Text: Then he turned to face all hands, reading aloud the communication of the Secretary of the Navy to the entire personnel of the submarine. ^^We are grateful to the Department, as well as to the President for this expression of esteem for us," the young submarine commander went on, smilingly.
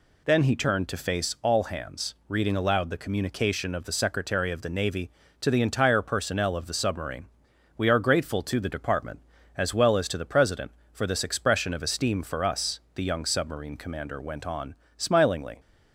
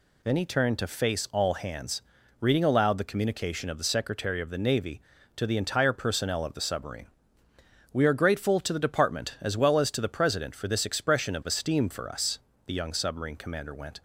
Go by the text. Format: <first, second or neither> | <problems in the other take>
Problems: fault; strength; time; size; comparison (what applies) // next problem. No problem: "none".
first | stops before "on smilingly"; at 13.9 s